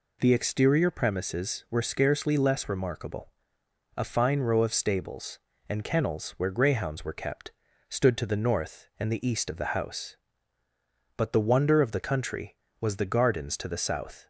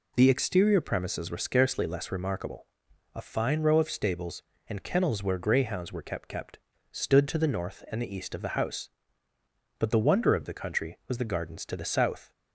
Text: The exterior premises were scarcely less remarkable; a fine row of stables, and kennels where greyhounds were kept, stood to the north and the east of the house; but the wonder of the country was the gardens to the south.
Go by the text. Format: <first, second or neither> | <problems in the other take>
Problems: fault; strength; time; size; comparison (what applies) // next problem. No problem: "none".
first | says "kept" twice; at 6.2 s